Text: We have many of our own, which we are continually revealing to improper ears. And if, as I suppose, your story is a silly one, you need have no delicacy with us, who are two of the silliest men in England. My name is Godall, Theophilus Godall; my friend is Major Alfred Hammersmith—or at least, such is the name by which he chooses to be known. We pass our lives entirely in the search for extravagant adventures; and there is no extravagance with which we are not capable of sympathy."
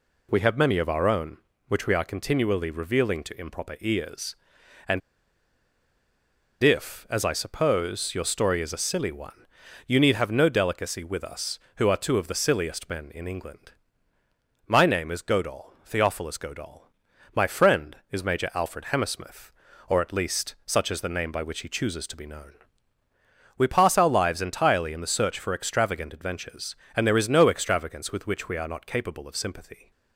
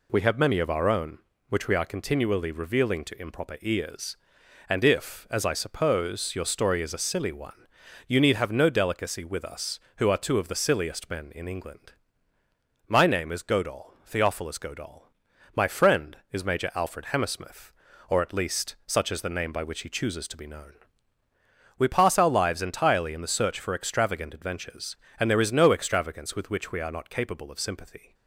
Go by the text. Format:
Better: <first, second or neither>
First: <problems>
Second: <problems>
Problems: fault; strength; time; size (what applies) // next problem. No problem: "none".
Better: second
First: pauses between "And" and "if"; strong; at 5.0 s; 1.6 s long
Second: none